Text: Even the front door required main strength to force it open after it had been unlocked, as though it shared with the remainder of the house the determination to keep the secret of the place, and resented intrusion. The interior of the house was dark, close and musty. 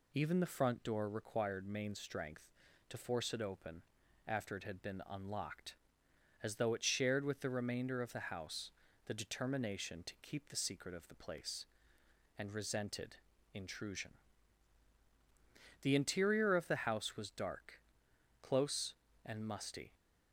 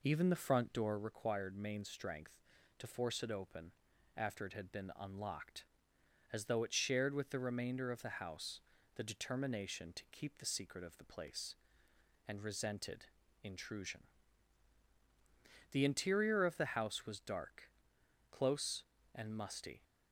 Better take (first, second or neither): first